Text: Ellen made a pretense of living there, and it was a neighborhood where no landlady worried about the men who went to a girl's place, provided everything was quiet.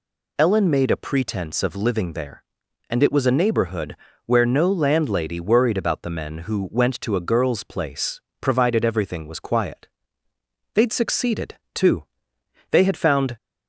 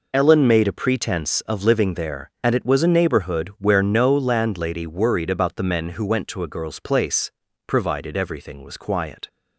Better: second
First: pauses between "neighborhood" and "where"; slight; at 3.9 s; 0.28 s long // goes on to say "They'd succeeded too they had found"; strong; from 10.7 s on; 2.6 s long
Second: none

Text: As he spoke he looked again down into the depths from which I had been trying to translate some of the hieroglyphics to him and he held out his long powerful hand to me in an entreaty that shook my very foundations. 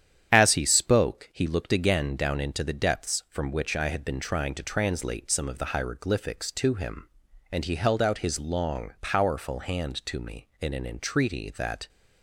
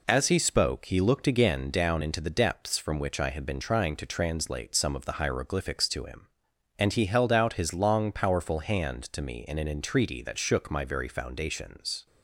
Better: second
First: starts louder than the rest; strong; until 1.3 s; 9.5 dB // stops before "shook my very foundations"; at 11.8 s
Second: none

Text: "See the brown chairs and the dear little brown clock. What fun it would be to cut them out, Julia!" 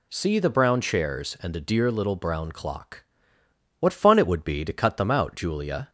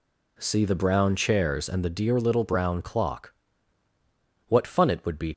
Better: first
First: none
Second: stops before "to cut them out Julia"; at 5.3 s

